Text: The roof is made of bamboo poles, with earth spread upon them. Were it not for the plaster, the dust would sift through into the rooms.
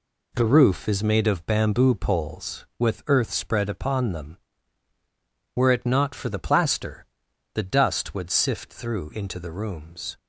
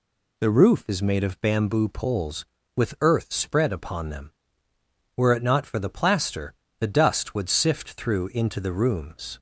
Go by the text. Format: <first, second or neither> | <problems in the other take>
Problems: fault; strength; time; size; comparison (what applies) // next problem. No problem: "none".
neither | none